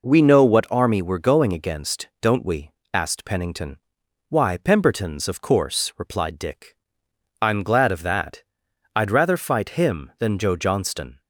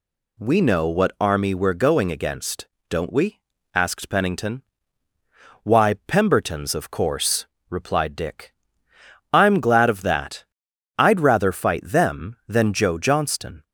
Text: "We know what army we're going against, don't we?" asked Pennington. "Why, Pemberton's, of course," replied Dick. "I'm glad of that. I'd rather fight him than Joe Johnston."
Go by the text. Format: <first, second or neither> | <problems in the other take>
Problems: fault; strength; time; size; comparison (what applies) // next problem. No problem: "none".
first | says "them" for "him"; at 11.8 s